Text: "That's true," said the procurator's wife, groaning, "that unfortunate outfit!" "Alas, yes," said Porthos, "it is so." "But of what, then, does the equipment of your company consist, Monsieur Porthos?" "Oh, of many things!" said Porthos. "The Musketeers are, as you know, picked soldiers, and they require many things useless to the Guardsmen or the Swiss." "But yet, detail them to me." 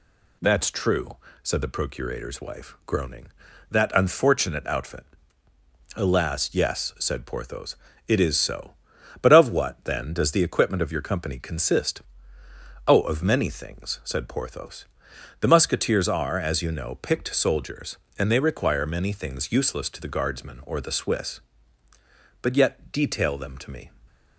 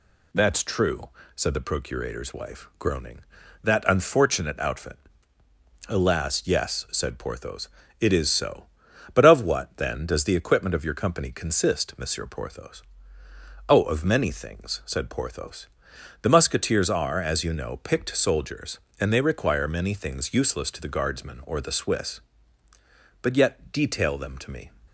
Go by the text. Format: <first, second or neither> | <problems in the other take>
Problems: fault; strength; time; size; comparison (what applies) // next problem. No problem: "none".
second | skips "Monsieur Porthos"; at 12.4 s